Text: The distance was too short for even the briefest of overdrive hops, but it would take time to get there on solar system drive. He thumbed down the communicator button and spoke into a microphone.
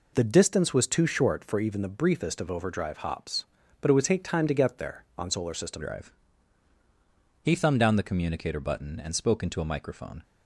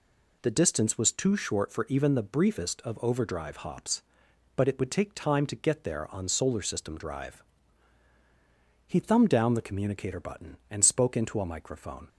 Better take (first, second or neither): second